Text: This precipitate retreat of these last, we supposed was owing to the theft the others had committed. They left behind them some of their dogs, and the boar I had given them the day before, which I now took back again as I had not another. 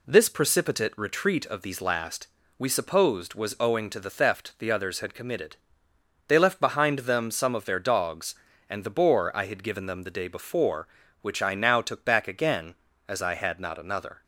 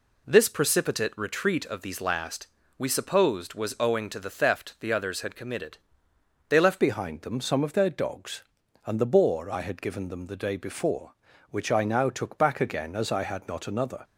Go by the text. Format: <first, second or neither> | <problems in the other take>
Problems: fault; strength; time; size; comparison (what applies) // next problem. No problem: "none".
first | changes voice at "behind"; from 6.7 s on; 7.3 s long